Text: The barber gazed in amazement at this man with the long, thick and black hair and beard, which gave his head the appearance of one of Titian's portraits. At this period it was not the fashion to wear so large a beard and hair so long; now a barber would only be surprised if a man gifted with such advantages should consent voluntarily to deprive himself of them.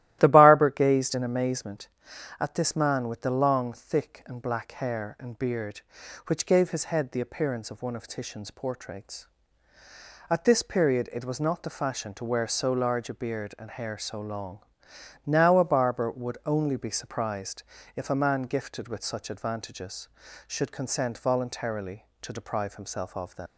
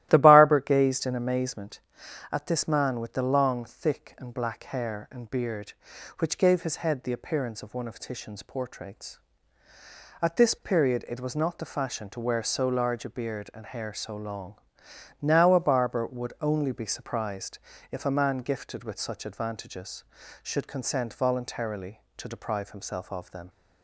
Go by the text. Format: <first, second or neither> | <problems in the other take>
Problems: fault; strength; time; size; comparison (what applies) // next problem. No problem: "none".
second | starts louder than the rest; strong; until 1.2 s; 14.5 dB; strong in the second // pauses between "surprised" and "if"; slight; at 17.6 s; 0.32 s long; slight in the second // leaves "them" unfinished; at 23.4 s; 75 ms